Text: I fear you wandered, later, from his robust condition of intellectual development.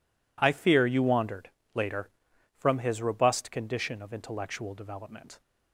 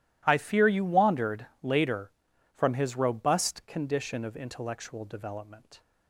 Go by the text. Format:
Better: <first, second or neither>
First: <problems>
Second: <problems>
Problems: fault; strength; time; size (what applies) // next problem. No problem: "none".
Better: neither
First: none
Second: none